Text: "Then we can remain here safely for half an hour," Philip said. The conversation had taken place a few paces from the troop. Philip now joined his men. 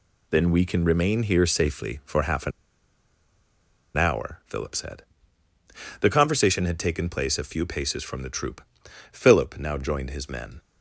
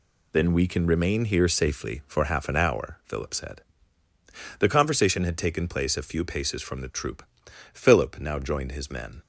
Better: second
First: pauses between "an" and "hour"; strong; at 2.5 s; 1.4 s long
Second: none

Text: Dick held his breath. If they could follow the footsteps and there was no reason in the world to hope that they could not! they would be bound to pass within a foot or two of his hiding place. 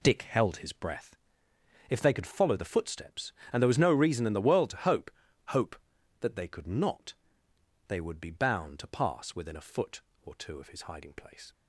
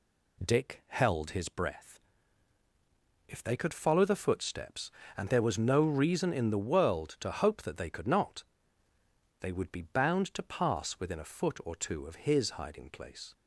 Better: second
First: says "hope" twice; at 5.4 s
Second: none

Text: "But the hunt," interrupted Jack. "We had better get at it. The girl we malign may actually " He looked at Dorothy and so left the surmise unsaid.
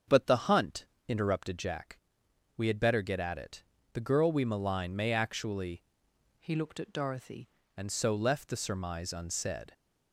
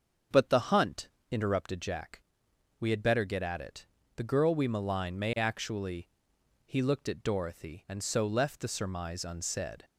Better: second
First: starts louder than the rest; strong; until 1.2 s; 7 dB // changes voice from "He" to "Dorothy"; from 6.3 to 7.4 s; 1.1 s long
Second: starts louder than the rest; until 1.5 s; 7 dB

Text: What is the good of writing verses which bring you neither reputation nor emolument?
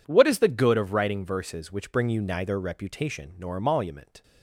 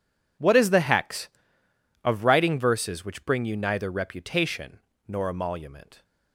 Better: first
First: none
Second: says "hex" for "good"; at 0.7 s // pauses between "reputation" and "nor"; slight; at 4.7 s; 0.28 s long

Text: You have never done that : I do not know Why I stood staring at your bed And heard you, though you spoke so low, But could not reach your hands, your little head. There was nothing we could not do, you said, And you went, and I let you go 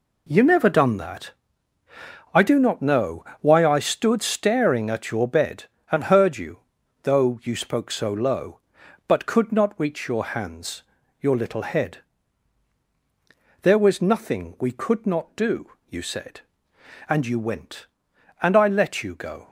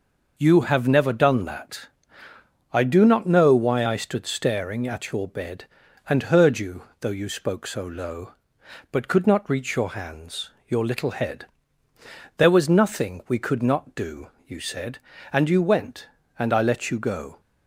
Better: second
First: skips "have"; at 0.4 s // pauses between "know" and "Why"; slight; at 3.2 s; 0.16 s long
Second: none

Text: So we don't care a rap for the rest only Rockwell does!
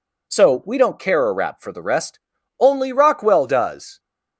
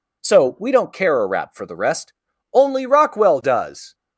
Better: neither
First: pauses between "rest" and "only"; at 2.1 s; 0.40 s long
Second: pauses between "rest" and "only"; at 2.1 s; 0.40 s long

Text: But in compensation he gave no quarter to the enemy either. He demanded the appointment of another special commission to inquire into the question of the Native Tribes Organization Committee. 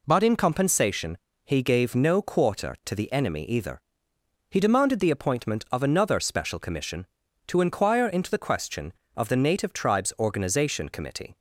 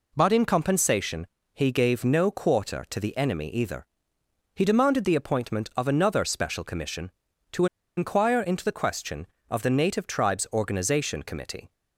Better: first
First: pauses between "compensation" and "he"; slight; at 1.1 s; 0.28 s long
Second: pauses between "compensation" and "he"; slight; at 1.2 s; 0.28 s long // pauses between "to" and "inquire"; slight; at 7.6 s; 0.31 s long

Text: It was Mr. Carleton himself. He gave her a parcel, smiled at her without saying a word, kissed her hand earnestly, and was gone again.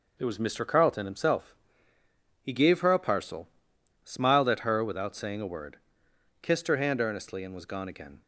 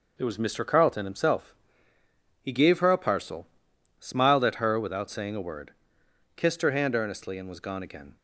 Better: neither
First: none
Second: none

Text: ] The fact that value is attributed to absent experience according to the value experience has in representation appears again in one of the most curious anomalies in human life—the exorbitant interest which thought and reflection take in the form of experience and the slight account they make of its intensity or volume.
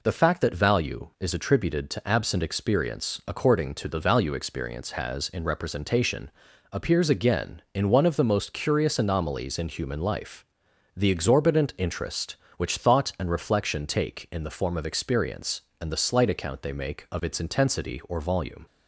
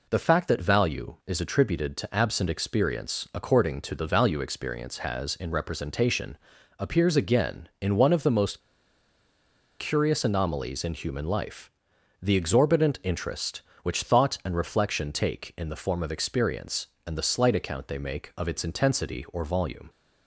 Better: first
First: pauses between "representation" and "appears"; at 6.3 s; 0.40 s long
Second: pauses between "representation" and "appears"; at 6.3 s; 0.40 s long // pauses between "most" and "curious"; at 8.5 s; 1.2 s long

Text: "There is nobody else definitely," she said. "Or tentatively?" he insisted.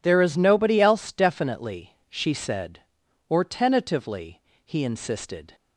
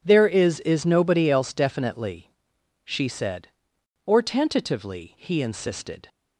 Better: first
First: none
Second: says "is" twice; at 0.5 s

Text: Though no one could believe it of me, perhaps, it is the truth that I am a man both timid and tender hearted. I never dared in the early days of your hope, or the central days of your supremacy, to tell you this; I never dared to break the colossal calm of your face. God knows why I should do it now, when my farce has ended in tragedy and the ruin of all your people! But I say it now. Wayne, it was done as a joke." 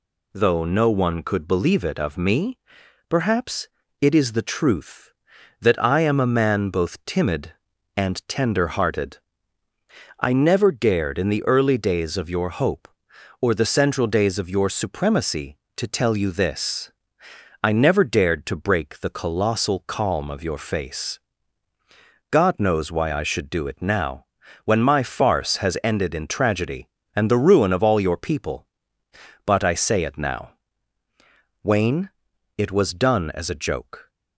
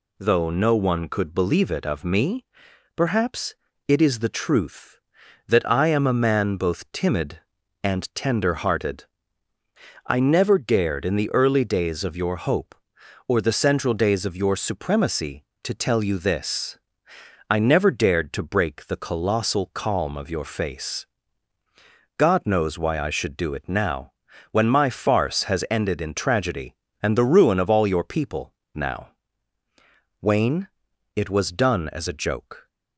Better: first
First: none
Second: skips "But I say it"; at 28.6 s

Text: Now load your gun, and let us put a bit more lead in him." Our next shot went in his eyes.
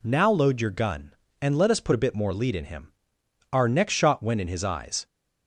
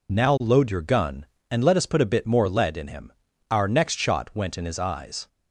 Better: first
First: none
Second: loses the start of "Now"; at 0.0 s; 50 ms

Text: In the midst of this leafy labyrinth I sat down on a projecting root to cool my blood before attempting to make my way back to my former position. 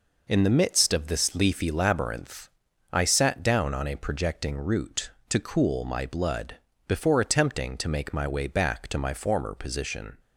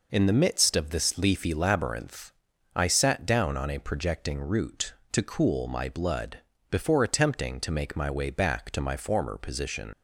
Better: first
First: pauses between "labyrinth" and "I"; at 2.4 s; 0.42 s long // pauses between "blood" and "before"; slight; at 6.5 s; 0.34 s long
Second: pauses between "labyrinth" and "I"; at 2.3 s; 0.42 s long // pauses between "blood" and "before"; slight; at 6.3 s; 0.34 s long // leaves "position" unfinished; at 9.9 s; 95 ms

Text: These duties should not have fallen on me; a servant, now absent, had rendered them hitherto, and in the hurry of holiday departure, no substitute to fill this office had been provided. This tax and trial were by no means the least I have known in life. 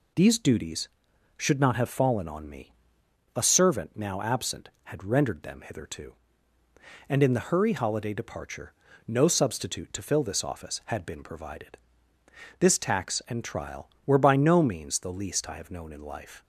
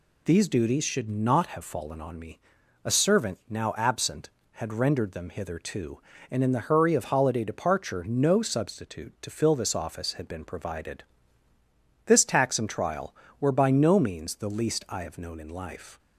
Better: second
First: skips "of"; at 7.7 s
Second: none

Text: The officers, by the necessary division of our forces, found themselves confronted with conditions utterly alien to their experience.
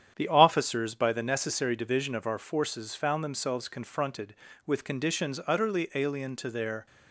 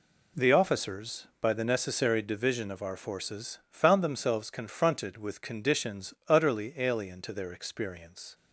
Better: second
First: starts louder than the rest; strong; until 1.1 s; 9 dB // stops before "experience"; at 6.8 s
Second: none

